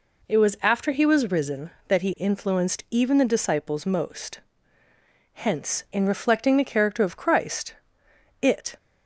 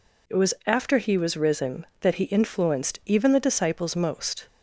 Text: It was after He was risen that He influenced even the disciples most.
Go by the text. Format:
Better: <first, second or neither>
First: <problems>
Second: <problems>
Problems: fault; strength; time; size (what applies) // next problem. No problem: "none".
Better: second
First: goes on to say "Hence in reflecting the character of Christ it"; strong; from 5.3 s on; 3.4 s long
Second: none